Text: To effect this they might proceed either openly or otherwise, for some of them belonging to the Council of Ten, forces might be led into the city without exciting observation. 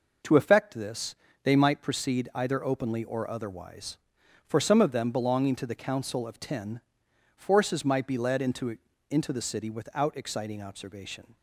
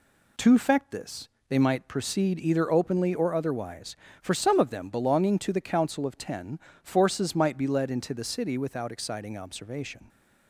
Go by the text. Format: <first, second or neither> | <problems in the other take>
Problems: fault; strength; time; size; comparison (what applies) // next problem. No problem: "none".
second | pauses between "this" and "they"; slight; at 1.1 s; 0.30 s long; slight in the second // says "into" twice; at 9.0 s